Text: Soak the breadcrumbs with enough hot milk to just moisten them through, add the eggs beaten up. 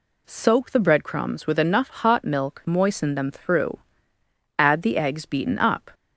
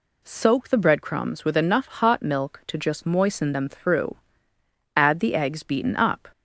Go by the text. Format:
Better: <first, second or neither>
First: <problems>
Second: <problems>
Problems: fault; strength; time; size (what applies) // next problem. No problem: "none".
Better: second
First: skips "to just"; at 2.6 s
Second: none